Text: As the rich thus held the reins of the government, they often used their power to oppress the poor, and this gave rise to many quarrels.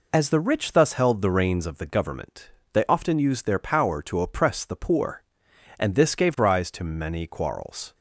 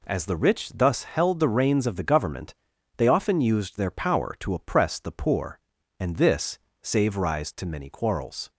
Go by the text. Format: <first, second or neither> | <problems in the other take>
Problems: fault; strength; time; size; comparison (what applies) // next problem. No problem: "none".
first | says "save" for "gave"; at 6.8 s